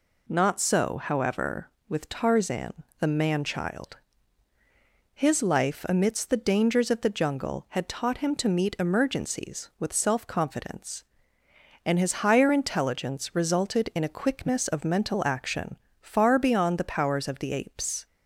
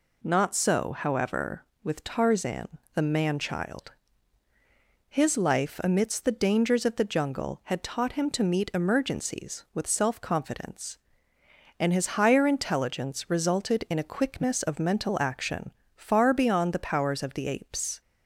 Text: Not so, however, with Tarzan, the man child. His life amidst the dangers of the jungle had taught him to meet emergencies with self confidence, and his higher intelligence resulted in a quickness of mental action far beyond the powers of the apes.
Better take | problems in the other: neither | pauses between "action" and "far"; slight; the same in both

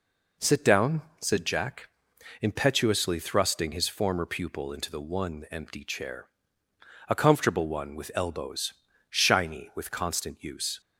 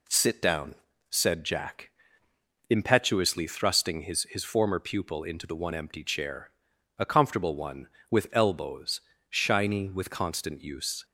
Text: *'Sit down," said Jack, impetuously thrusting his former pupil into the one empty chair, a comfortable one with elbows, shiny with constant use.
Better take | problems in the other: first | says "his" twice; at 4.2 s

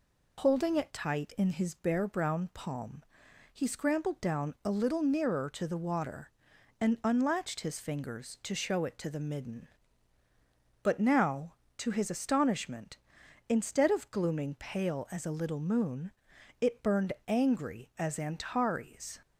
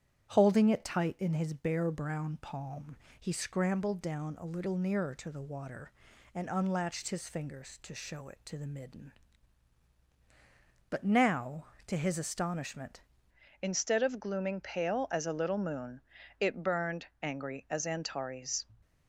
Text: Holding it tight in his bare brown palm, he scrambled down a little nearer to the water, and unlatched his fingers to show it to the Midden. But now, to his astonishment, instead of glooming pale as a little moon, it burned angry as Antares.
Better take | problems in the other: first | starts louder than the rest; strong; until 1.3 s; 9.5 dB // changes voice at "instead"; from 13.6 s on; 5.0 s long // pauses between "burned" and "angry"; slight; at 17.0 s; 0.16 s long

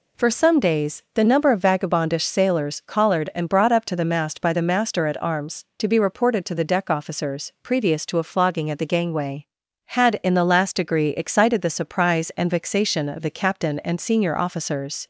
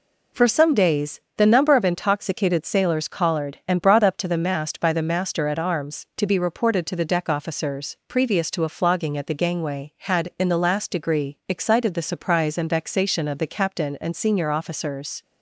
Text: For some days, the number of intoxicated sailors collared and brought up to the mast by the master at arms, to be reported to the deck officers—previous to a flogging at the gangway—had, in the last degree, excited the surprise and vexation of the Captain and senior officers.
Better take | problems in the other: second | says "vagabondish" for "intoxicated"; at 1.5 s

